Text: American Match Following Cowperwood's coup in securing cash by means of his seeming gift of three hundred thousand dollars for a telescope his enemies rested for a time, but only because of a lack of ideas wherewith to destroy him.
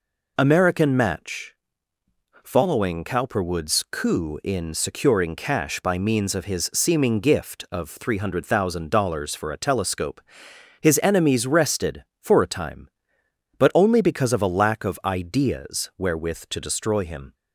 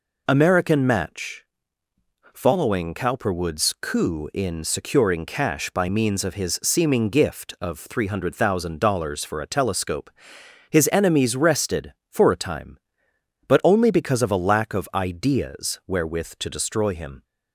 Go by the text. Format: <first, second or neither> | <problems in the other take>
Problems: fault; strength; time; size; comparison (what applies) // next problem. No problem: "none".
neither | pauses between "Match" and "Following"; noticeable; the same in both // pauses between "telescope" and "his"; noticeable; the same in both